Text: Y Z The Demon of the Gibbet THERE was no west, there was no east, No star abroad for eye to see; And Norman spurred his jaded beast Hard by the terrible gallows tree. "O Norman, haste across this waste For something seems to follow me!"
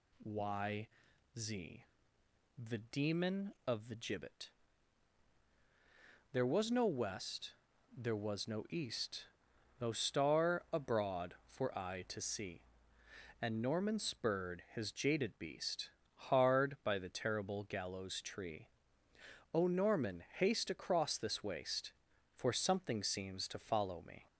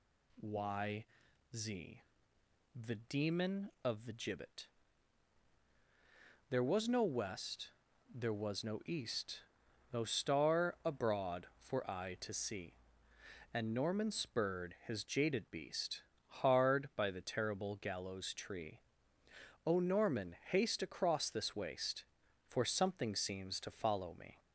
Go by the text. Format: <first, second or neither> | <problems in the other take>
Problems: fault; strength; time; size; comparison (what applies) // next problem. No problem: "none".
neither | pauses between "Y" and "Z"; noticeable; the same in both // pauses between "Z" and "The"; noticeable; the same in both // pauses between "Gibbet" and "THERE"; strong; the same in both // pauses between "beast" and "Hard"; slight; the same in both